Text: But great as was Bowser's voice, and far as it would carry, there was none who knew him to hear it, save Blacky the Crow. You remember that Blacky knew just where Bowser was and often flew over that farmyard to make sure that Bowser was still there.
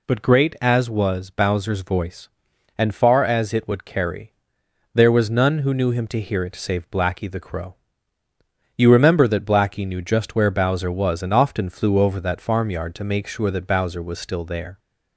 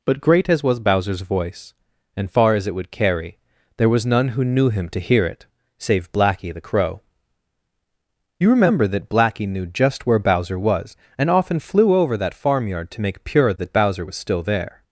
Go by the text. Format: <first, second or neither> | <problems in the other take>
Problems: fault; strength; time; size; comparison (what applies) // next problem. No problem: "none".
first | says "pure" for "sure"; at 13.2 s